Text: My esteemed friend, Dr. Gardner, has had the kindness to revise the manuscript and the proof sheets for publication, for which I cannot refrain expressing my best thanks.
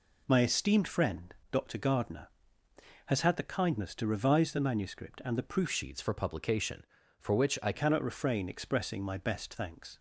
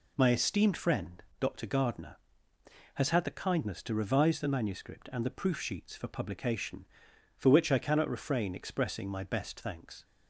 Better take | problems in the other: second | changes voice from "sheets" to "I"; from 5.6 to 7.7 s; 2.1 s long

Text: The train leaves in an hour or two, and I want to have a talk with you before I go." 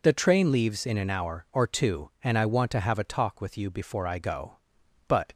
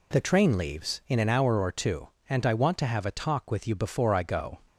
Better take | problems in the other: second | goes on to say "But"; slight; from 5.0 s on; 0.26 s long

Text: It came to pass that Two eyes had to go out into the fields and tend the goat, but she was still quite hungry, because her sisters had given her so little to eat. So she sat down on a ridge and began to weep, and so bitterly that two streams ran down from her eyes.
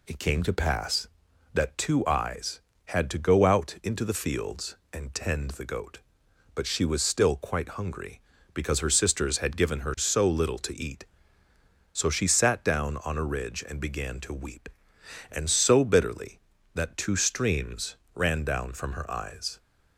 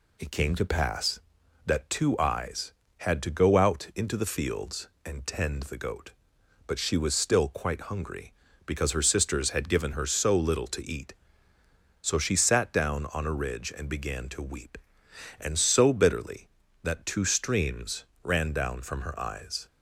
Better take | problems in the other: neither | pauses between "streams" and "ran"; slight; the same in both

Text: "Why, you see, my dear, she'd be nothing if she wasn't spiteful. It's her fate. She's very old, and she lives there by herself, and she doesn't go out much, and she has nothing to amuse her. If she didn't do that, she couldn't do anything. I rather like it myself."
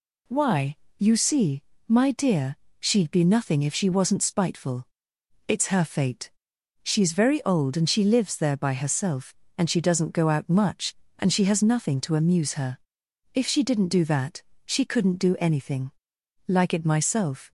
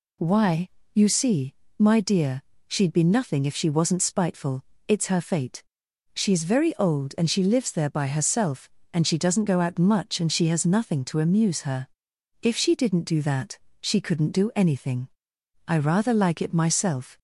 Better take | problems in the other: second | skips "I rather"; at 16.1 s

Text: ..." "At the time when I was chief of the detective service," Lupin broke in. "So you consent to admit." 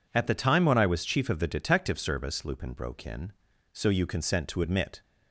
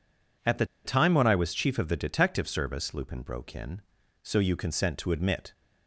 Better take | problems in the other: first | pauses between "the" and "time"; slight; at 0.6 s; 0.20 s long

